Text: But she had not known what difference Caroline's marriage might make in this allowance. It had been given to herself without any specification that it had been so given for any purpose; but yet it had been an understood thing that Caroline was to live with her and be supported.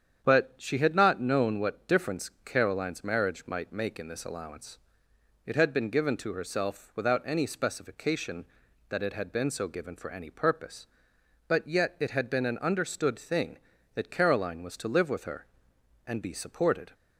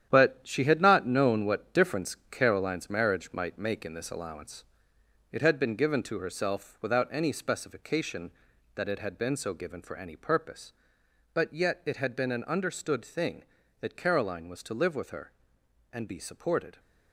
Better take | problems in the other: first | gets quieter; strong; throughout; 8.5 dB // starts louder than the rest; strong; until 1.1 s; 10 dB; strong in the first

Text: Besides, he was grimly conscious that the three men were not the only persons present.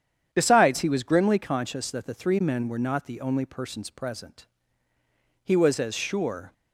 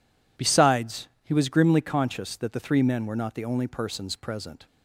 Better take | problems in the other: second | starts louder than the rest; strong; until 1.3 s; 8.5 dB // goes on to say "He was as sure"; noticeable; from 5.4 s on; 1.0 s long

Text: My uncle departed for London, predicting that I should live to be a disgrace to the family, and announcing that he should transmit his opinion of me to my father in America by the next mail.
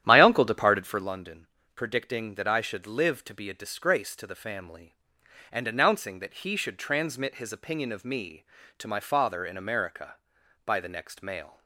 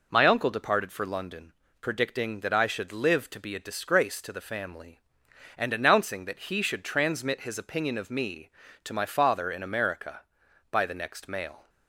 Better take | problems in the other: second | starts louder than the rest; strong; until 1.1 s; 10.5 dB

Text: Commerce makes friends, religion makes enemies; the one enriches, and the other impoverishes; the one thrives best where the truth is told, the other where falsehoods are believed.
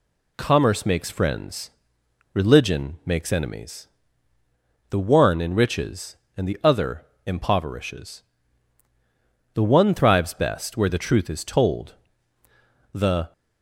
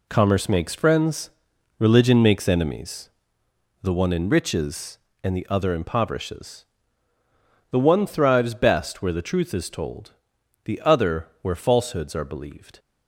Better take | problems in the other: second | pauses between "other" and "impoverishes"; slight; at 7.0 s; 0.18 s long // stops before "other where falsehoods are believed"; at 13.3 s

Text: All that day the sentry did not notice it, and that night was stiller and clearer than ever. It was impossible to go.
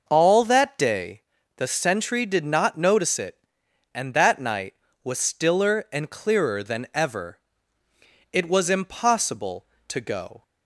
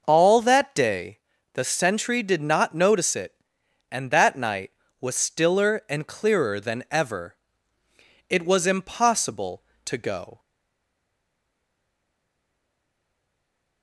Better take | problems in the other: first | pauses between "day" and "the"; slight; at 1.1 s; 0.34 s long; slight in the first // stays silent after the last word; strong; from 10.3 s on; 3.5 s long

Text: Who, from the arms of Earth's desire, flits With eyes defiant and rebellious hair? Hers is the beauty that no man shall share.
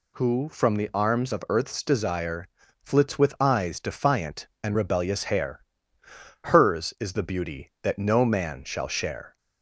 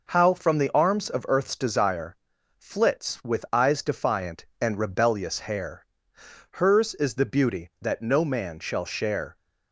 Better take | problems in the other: first | says "How" for "Who"; at 0.1 s

